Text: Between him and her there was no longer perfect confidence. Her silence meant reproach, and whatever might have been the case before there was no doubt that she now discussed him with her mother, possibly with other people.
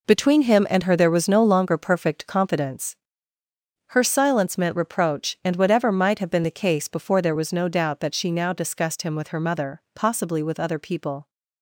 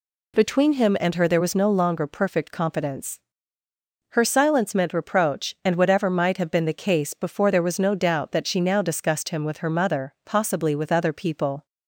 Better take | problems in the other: second | gets quieter; strong; throughout; 9.5 dB

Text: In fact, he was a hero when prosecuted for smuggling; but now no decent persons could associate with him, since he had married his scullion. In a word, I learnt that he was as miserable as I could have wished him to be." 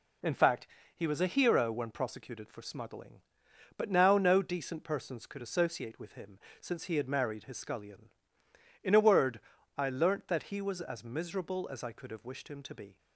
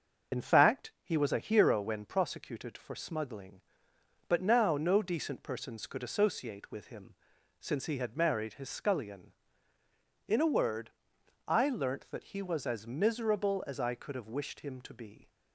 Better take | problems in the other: first | loses the start of "In"; at 0.3 s; 40 ms // starts louder than the rest; until 1.4 s; 6.5 dB

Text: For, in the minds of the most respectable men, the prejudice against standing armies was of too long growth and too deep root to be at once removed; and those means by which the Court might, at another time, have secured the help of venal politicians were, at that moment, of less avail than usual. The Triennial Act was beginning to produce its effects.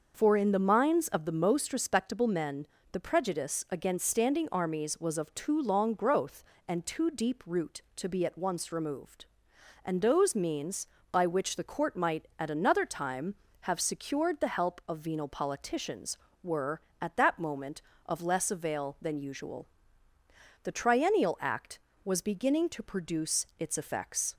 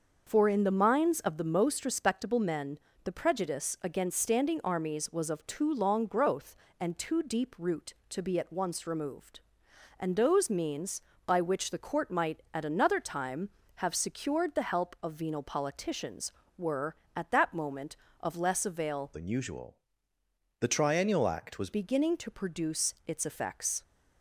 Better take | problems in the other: first | starts louder than the rest; until 1.2 s; 6 dB; also in the first // changes voice from "than" to "was"; from 19.1 to 21.7 s; 2.6 s long

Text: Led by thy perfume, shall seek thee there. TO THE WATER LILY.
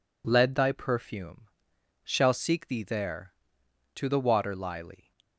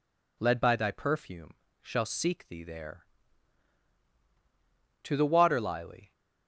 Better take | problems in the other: second | skips "by"; at 0.5 s

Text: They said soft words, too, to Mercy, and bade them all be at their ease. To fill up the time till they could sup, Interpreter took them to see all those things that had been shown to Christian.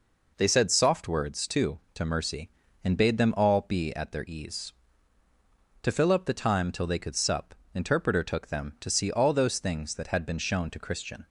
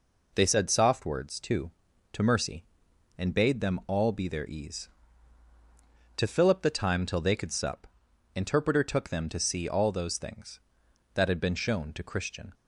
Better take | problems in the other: first | skips "at"; at 4.2 s

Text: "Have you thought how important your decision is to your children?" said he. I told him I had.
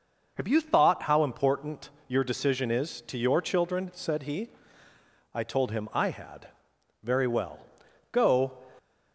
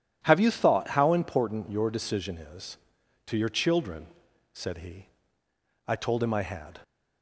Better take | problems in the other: second | pauses between "important" and "your"; slight; at 1.8 s; 0.20 s long // goes on to say "Very well Go"; from 7.0 s on; 1.5 s long

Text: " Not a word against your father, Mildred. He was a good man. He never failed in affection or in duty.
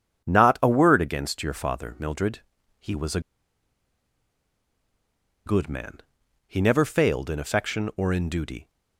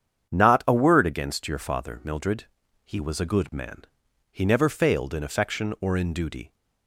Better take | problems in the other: second | starts louder than the rest; strong; until 1.2 s; 8 dB; strong in the second // pauses between "a" and "good"; strong; at 3.1 s; 2.2 s long

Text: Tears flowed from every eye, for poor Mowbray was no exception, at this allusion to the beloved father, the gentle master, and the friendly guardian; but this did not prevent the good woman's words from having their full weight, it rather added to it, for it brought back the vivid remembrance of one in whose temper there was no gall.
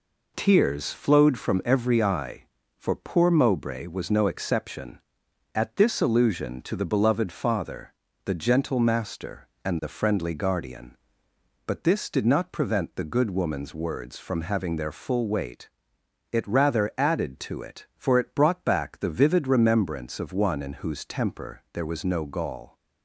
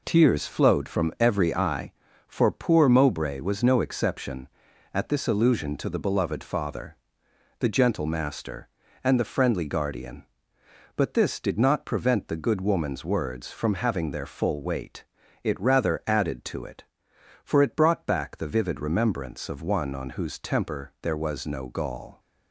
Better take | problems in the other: first | says "on" for "in"; at 19.9 s

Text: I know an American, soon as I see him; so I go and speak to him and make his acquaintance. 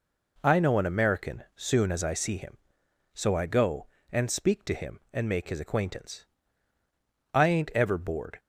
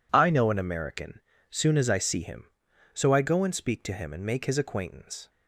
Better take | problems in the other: second | goes on to say "I ain't ever bored"; noticeable; from 7.3 s on; 1.0 s long

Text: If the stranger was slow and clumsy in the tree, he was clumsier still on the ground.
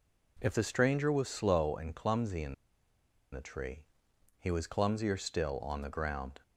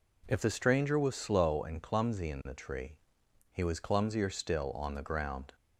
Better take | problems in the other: second | pauses between "in" and "the"; noticeable; at 2.5 s; 0.78 s long

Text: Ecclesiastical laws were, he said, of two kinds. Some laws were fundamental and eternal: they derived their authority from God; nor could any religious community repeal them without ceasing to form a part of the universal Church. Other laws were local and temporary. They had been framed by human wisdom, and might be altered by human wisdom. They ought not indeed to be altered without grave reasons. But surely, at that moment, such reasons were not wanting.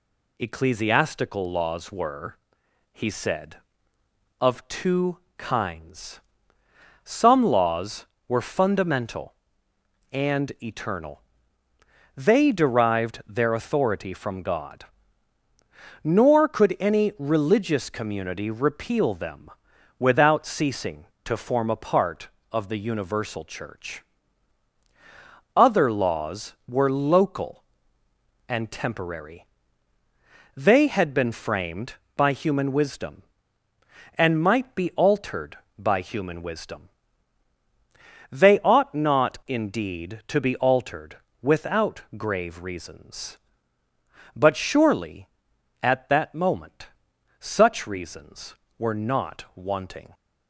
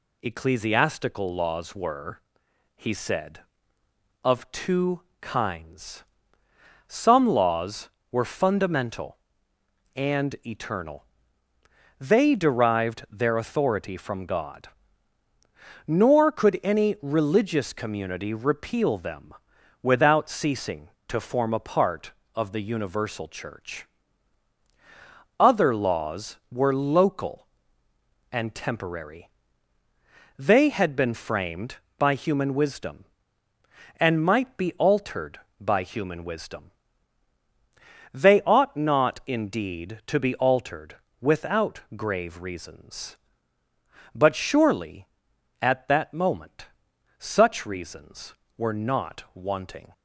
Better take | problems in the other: neither | pauses between "two" and "kinds"; slight; the same in both // pauses between "them" and "without"; noticeable; the same in both // pauses between "altered" and "without"; slight; the same in both // pauses between "without" and "grave"; slight; the same in both

